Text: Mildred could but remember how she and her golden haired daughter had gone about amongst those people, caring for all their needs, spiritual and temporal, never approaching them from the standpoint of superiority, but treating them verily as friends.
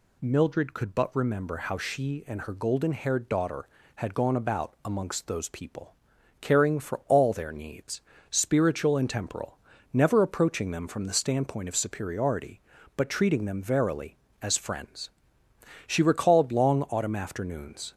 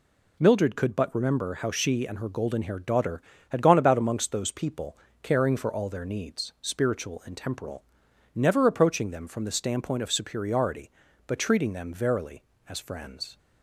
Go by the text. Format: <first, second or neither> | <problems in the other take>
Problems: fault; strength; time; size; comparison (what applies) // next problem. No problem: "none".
second | goes on to say "She recalled long autumn afternoons"; strong; from 15.8 s on; 2.0 s long